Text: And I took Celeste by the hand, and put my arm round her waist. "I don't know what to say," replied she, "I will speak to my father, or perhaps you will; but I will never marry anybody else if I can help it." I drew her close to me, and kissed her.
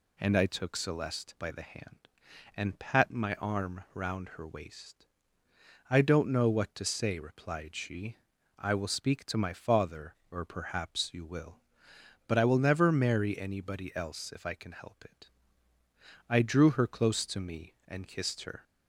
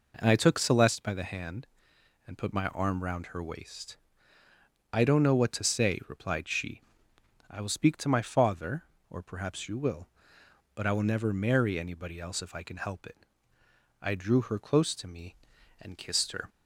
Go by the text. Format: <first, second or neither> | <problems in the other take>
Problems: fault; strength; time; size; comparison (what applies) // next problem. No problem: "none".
second | says "pat" for "put"; at 2.7 s